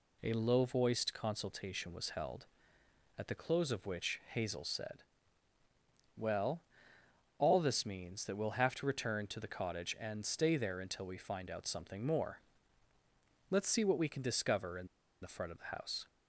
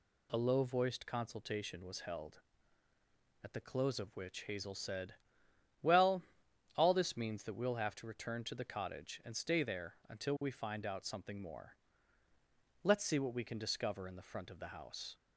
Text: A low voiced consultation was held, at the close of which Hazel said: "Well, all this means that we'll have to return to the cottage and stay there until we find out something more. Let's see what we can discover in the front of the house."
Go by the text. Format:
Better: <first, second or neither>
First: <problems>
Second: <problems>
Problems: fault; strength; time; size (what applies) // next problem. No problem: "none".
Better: second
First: pauses between "in" and "the"; slight; at 14.8 s; 0.34 s long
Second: none